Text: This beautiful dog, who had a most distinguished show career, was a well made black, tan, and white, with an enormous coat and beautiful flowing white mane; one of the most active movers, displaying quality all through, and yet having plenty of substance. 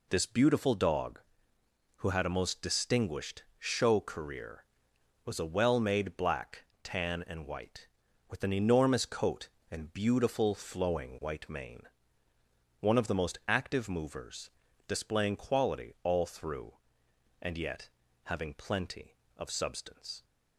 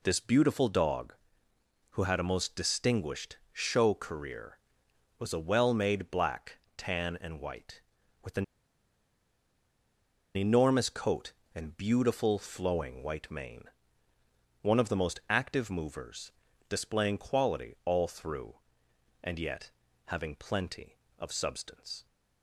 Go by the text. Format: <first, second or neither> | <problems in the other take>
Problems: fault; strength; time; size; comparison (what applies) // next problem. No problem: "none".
first | pauses between "distinguished" and "show"; slight; at 3.3 s; 0.16 s long; slight in the first // pauses between "an" and "enormous"; strong; at 8.4 s; 1.9 s long // pauses between "yet" and "having"; slight; at 19.6 s; 0.36 s long; slight in the first